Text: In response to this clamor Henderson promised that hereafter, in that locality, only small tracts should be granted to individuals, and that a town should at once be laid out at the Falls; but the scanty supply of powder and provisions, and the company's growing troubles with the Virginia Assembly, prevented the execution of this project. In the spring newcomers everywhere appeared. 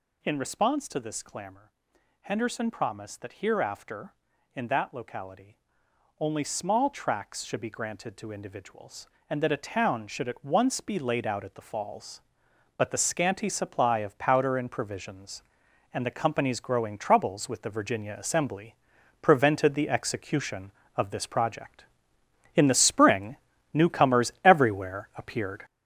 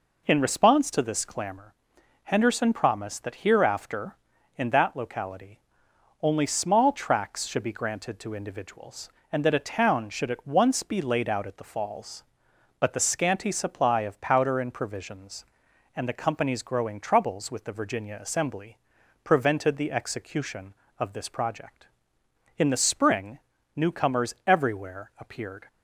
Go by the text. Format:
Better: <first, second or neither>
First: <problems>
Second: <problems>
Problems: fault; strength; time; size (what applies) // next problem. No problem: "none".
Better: second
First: gets louder; throughout; 7 dB // pauses between "clamor" and "Henderson"; noticeable; at 1.7 s; 0.50 s long // pauses between "spring" and "newcomers"; slight; at 23.3 s; 0.36 s long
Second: pauses between "clamor" and "Henderson"; noticeable; at 1.7 s; 0.50 s long // pauses between "spring" and "newcomers"; slight; at 23.3 s; 0.36 s long